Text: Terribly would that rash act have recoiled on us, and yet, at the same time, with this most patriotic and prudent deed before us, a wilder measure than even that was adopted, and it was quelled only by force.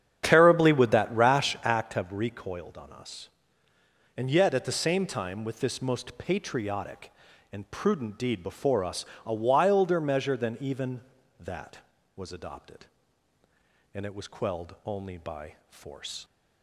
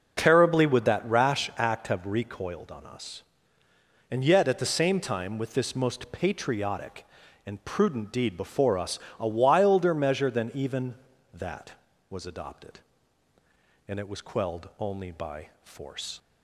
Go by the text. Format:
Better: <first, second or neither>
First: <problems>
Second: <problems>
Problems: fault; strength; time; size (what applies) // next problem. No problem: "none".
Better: second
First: starts louder than the rest; strong; until 2.0 s; 8.5 dB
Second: none